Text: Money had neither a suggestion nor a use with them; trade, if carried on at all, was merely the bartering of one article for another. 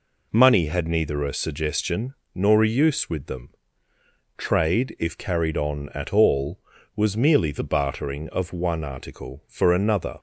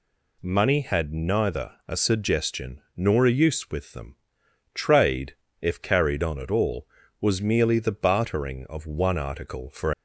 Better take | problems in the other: first | pauses between "suggestion" and "nor"; slight; at 2.7 s; 0.16 s long; slight in the first // stops before "another"; at 9.9 s

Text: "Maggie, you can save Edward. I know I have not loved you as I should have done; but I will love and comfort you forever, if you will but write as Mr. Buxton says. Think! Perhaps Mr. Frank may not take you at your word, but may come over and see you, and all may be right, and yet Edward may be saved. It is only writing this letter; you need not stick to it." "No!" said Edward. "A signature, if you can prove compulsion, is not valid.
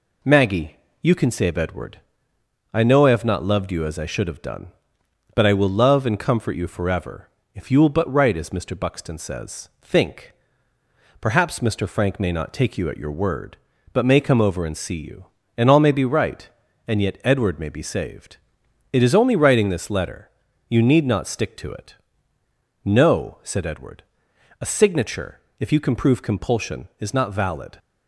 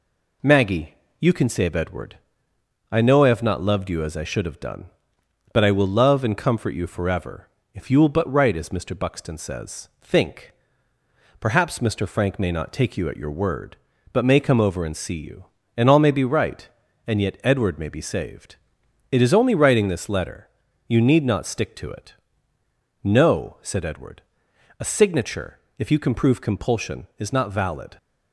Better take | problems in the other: neither | none

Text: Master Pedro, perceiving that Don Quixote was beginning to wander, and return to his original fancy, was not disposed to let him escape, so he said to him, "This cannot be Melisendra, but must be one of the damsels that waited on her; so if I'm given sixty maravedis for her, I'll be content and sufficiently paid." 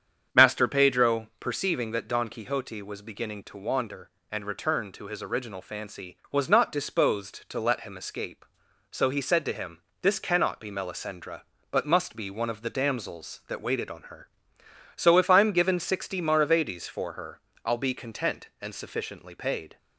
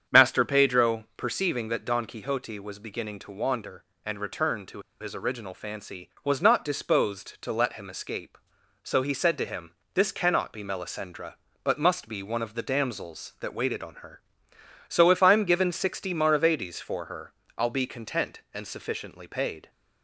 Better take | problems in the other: first | starts louder than the rest; strong; until 1.2 s; 7.5 dB; strong in the first // pauses between "to" and "his"; slight; at 4.7 s; 0.21 s long

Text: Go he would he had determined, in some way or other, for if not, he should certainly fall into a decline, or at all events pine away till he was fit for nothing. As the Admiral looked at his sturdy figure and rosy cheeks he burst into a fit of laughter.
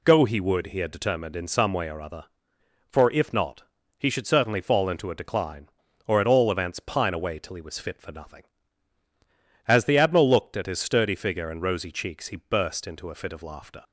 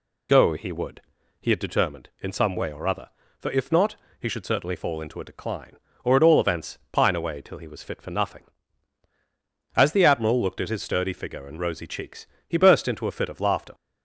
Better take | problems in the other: first | loses the start of "Go"; at 0.2 s; 35 ms // pauses between "would" and "he"; at 1.0 s; 0.40 s long // pauses between "cheeks" and "he"; slight; at 12.2 s; 0.22 s long

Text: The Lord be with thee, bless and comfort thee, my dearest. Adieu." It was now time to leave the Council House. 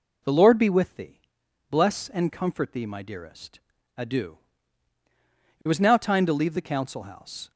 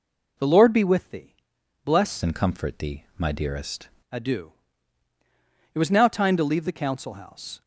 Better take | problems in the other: first | changes voice from "and" to "dearest"; from 2.2 to 3.8 s; 1.6 s long

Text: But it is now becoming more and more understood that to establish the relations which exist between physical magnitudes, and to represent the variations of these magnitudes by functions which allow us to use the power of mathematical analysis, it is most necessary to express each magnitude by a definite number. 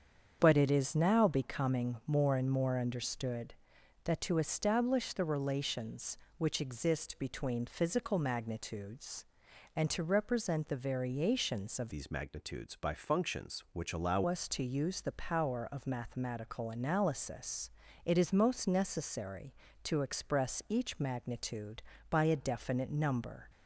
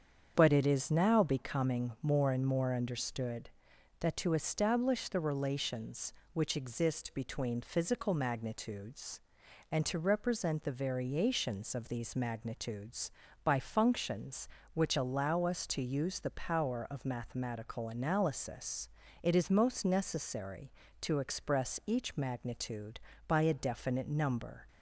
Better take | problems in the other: second | starts louder than the rest; strong; until 1.4 s; 7.5 dB; strong in the second // changes voice from "these" to "allow"; from 11.9 to 14.2 s; 2.3 s long

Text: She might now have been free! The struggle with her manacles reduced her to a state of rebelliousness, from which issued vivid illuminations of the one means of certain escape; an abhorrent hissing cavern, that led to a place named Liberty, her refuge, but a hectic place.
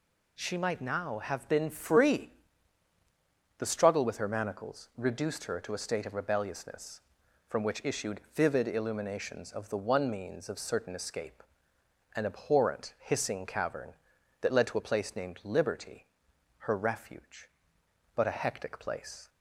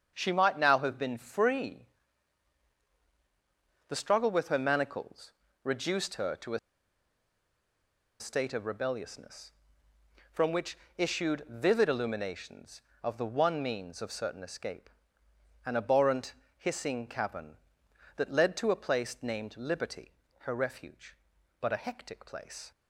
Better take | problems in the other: first | starts louder than the rest; strong; until 1.1 s; 7.5 dB // pauses between "manacles" and "reduced"; slight; at 5.3 s; 0.32 s long // pauses between "a" and "state"; strong; at 6.5 s; 1.6 s long // pauses between "which" and "issued"; slight; at 10.7 s; 0.20 s long // pauses between "abhorrent" and "hissing"; slight; at 16.3 s; 0.24 s long

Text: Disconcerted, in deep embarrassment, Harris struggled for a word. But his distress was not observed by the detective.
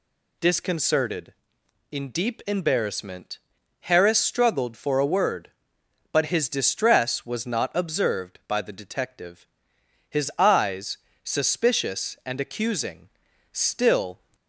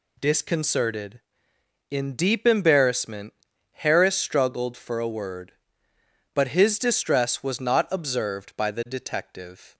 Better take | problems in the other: second | goes on to say "His eyes suspicious and accusing still"; strong; from 10.0 s on; 4.1 s long

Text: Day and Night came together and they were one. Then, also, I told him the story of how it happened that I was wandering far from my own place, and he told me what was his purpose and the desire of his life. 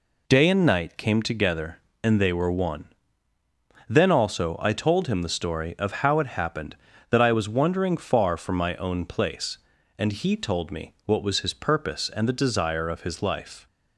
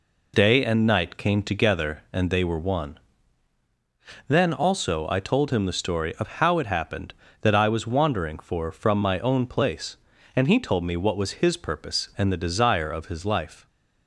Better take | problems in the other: first | says "for" for "far"; at 8.3 s

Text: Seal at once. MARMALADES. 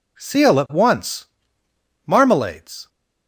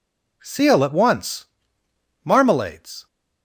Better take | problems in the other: neither | none

